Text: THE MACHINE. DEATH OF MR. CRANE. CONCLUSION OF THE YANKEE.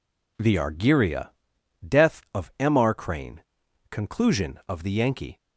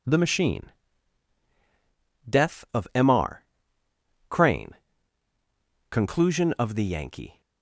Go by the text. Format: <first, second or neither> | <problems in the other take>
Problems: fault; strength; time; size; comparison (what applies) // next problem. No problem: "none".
second | says "Argyria" for "MACHINE"; at 0.5 s